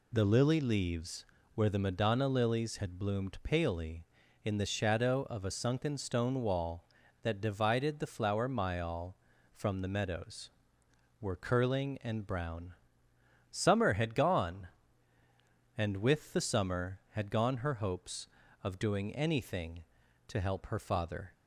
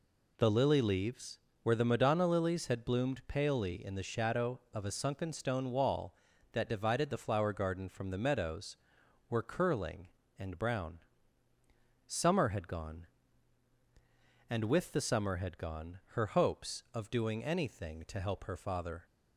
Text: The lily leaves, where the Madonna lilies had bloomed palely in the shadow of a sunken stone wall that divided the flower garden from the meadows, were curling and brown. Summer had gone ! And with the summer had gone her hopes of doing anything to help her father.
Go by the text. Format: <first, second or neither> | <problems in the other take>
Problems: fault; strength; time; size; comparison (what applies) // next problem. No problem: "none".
second | says "myall" for "garden"; at 8.4 s